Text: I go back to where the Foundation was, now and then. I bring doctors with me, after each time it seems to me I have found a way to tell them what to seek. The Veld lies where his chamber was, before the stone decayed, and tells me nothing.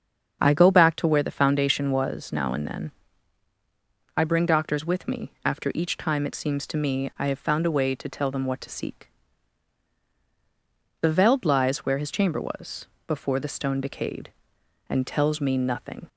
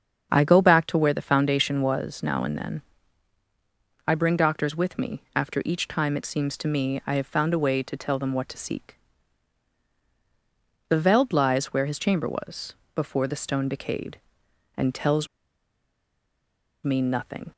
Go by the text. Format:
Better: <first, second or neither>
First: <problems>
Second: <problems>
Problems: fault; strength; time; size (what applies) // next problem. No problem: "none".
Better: first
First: starts louder than the rest; strong; until 1.4 s; 7 dB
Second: starts louder than the rest; strong; until 1.3 s; 7 dB // pauses between "tells" and "me"; strong; at 15.2 s; 1.5 s long